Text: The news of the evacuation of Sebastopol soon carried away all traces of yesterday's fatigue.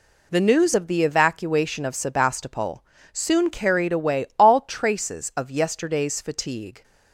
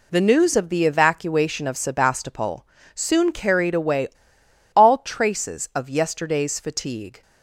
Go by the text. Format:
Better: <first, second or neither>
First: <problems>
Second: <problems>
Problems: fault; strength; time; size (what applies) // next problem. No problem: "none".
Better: first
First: pauses between "Sebastopol" and "soon"; slight; at 2.8 s; 0.30 s long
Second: pauses between "Sebastopol" and "soon"; slight; at 2.6 s; 0.30 s long // pauses between "away" and "all"; noticeable; at 4.0 s; 0.67 s long